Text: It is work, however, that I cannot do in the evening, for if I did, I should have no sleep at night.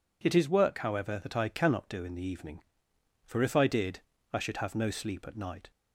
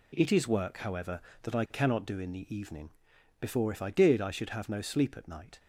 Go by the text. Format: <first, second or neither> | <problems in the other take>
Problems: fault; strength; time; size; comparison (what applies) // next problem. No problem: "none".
first | says "before" for "for"; at 3.3 s